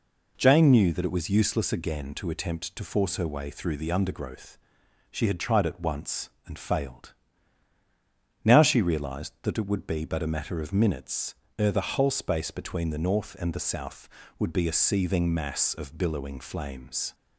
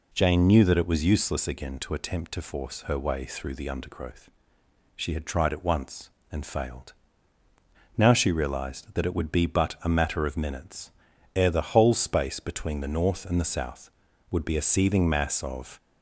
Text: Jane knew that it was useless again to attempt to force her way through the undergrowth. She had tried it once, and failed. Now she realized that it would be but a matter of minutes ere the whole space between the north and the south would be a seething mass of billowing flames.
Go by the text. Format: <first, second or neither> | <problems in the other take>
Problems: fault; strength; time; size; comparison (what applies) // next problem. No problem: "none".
first | pauses between "minutes" and "ere"; at 10.9 s; 0.44 s long; slight in the first // stops before "billowing flames"; at 15.7 s